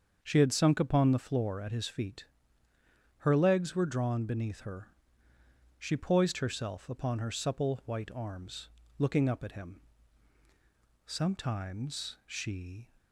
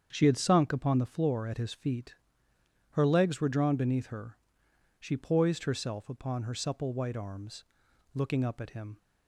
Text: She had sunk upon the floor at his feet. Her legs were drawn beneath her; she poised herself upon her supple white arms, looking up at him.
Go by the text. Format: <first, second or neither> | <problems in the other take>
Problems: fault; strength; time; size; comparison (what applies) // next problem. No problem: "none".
second | starts louder than the rest; until 1.2 s; 6.5 dB; strong in the second // goes on to say "Sometimes she"; strong; from 11.0 s on; 1.8 s long